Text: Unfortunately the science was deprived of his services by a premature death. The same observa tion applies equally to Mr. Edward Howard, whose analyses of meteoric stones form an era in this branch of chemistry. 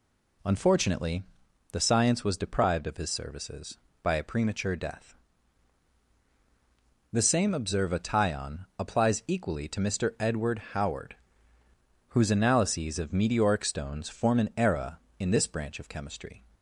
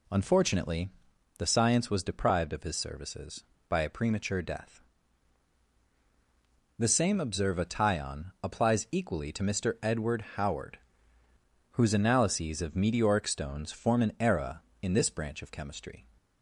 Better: neither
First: pauses between "Unfortunately" and "the"; noticeable; at 1.2 s; 0.48 s long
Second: pauses between "Unfortunately" and "the"; noticeable; at 0.8 s; 0.48 s long

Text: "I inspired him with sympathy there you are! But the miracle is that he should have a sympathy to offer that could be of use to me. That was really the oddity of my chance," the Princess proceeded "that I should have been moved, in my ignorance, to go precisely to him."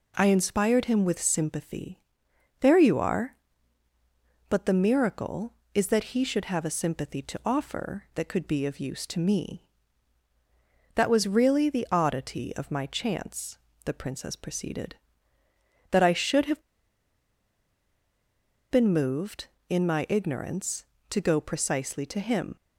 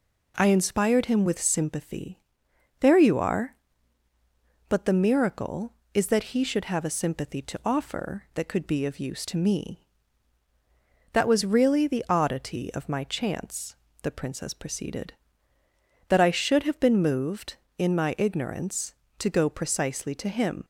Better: second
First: pauses between "sympathy" and "there"; noticeable; at 2.0 s; 0.60 s long // pauses between "have" and "been"; strong; at 16.6 s; 2.0 s long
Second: pauses between "sympathy" and "there"; noticeable; at 2.2 s; 0.60 s long

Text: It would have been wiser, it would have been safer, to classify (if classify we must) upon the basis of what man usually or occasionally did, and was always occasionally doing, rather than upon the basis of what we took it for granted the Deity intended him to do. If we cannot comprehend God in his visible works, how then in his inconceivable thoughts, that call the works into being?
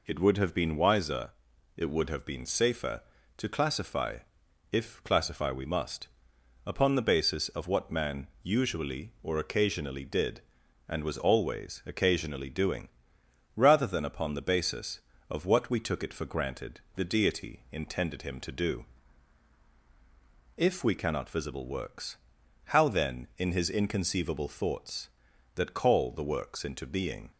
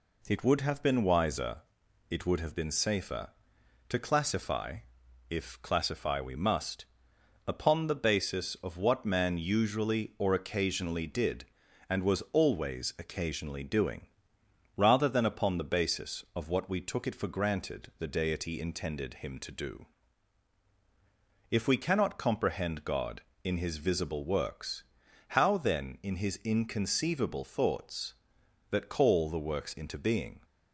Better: second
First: pauses between "man" and "usually"; slight; at 8.2 s; 0.16 s long // pauses between "granted" and "the"; slight; at 16.8 s; 0.16 s long // skips "comprehend God in his"; at 21.3 s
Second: none

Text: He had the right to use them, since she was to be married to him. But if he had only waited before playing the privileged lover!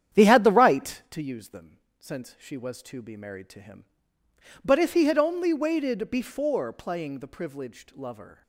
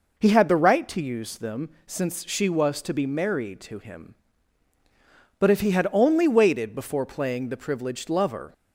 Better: second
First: starts louder than the rest; strong; until 1.2 s; 9.5 dB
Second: none

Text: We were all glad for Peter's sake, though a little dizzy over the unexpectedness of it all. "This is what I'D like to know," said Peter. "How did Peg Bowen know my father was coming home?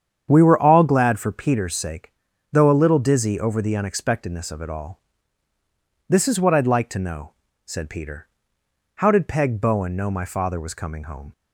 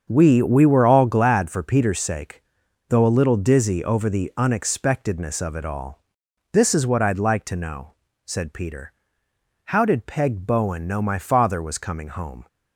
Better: first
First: starts louder than the rest; strong; until 1.3 s; 8.5 dB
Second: starts louder than the rest; strong; until 1.1 s; 7 dB // says "We" twice; at 0.4 s

